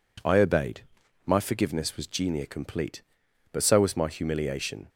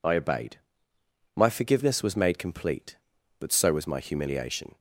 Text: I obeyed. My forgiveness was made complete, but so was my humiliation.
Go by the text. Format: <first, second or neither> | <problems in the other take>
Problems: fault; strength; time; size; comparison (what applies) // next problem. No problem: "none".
second | says "genia" for "made"; at 2.0 s